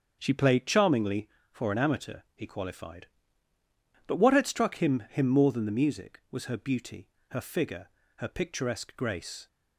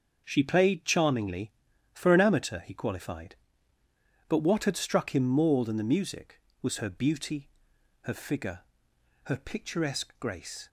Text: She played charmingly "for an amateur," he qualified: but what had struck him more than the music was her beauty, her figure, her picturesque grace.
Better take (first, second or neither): second